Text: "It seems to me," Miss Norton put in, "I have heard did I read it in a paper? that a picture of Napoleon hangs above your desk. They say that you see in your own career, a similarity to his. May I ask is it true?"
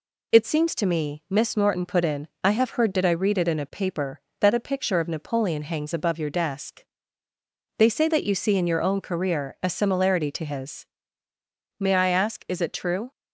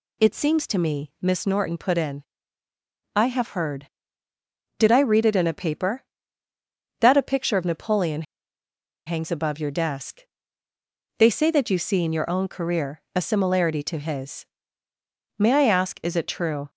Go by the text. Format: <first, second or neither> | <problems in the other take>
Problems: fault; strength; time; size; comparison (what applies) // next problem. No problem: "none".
first | pauses between "Napoleon" and "hangs"; noticeable; at 8.2 s; 0.84 s long